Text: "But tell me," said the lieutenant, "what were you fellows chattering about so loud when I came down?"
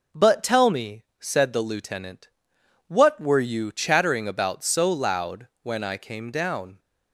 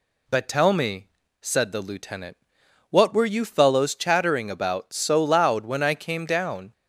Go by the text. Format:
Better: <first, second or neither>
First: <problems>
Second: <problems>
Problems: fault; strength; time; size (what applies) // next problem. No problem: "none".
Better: second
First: skips "fellows"; at 3.7 s // pauses between "loud" and "when"; slight; at 5.4 s; 0.16 s long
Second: none